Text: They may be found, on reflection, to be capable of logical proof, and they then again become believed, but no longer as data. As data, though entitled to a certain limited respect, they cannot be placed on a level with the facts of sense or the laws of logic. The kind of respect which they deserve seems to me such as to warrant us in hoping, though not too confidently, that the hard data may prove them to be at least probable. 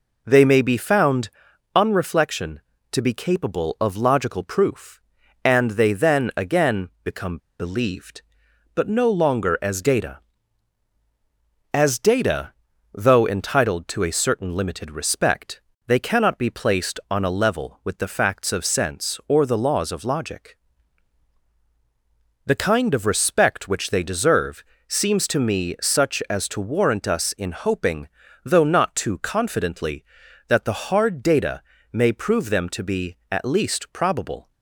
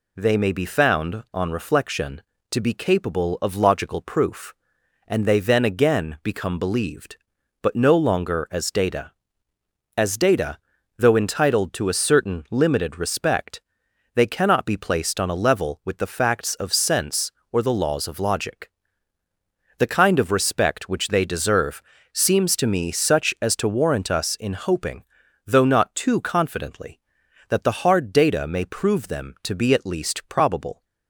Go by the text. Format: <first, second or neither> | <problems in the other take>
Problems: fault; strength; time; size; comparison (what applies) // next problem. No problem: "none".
second | pauses between "become" and "believed"; slight; at 7.3 s; 0.21 s long // pauses between "deserve" and "seems"; slight; at 24.6 s; 0.24 s long; slight in the second // pauses between "data" and "may"; slight; at 31.6 s; 0.32 s long